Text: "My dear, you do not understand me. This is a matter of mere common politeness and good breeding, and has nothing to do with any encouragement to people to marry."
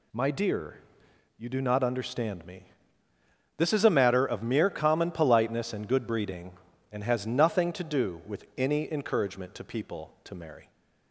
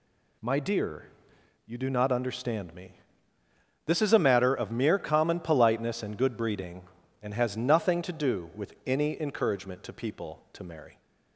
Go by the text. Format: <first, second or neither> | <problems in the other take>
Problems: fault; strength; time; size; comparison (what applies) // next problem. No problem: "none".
neither | none